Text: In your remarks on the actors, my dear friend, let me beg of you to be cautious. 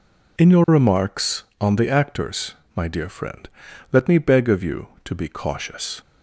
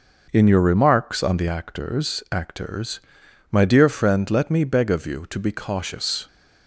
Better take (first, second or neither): first